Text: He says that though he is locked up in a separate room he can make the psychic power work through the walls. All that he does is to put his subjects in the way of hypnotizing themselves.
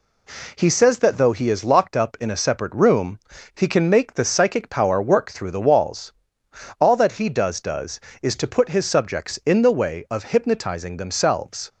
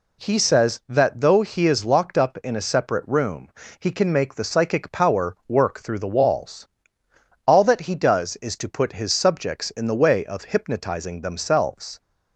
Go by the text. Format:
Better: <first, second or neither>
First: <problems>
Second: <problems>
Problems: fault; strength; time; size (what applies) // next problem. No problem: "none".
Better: second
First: pauses between "room" and "he"; slight; at 3.1 s; 0.34 s long // says "does" twice; at 7.5 s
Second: pauses between "room" and "he"; slight; at 3.4 s; 0.32 s long